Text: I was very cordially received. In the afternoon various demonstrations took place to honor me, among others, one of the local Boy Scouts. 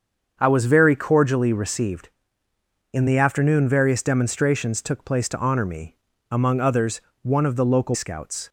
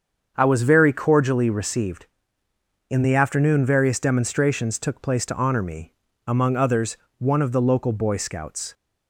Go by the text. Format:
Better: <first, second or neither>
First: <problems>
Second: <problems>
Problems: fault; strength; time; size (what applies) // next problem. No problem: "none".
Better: second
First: starts louder than the rest; until 1.4 s; 7 dB // skips "Boy"; at 7.9 s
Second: starts louder than the rest; until 1.3 s; 7 dB